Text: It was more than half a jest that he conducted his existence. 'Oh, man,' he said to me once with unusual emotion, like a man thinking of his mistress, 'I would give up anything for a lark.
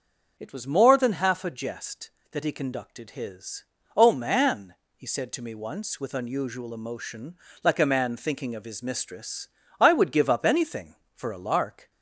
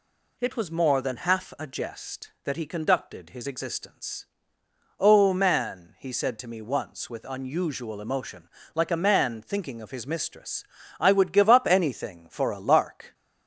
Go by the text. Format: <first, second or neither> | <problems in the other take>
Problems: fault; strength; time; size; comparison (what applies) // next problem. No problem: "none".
second | starts louder than the rest; until 1.3 s; 6 dB // skips "existence"; at 3.7 s